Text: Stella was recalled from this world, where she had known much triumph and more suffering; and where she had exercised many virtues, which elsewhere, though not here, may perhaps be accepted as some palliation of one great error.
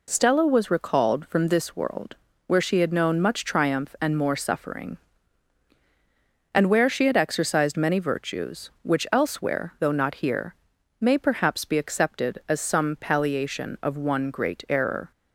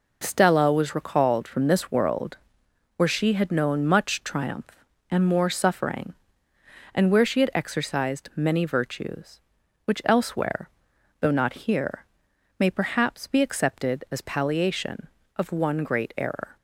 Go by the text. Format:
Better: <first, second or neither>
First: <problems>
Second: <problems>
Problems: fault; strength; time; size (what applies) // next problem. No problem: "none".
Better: first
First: none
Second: skips "some"; at 14.2 s